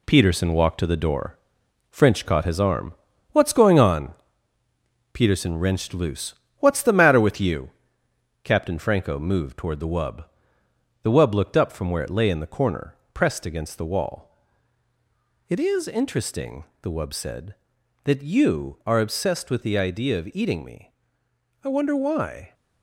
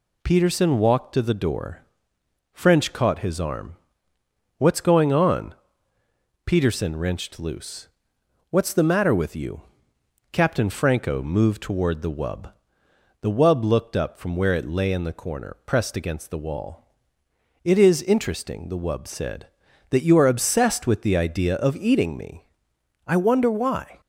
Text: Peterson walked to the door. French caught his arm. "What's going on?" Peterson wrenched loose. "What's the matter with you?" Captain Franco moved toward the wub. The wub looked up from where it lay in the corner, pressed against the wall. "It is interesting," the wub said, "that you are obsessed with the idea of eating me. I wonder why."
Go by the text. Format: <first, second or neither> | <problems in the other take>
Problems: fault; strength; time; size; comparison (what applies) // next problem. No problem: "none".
second | gets quieter; noticeable; throughout; 6 dB